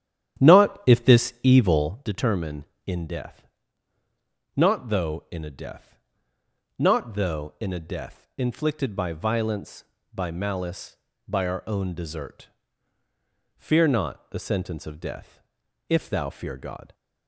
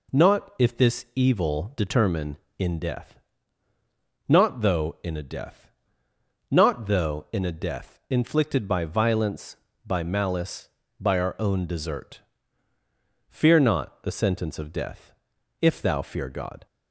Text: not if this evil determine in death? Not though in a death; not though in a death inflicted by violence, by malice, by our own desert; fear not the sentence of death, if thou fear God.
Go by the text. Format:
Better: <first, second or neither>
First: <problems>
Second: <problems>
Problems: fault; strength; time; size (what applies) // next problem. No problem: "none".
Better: second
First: starts louder than the rest; strong; until 1.9 s; 10 dB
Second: none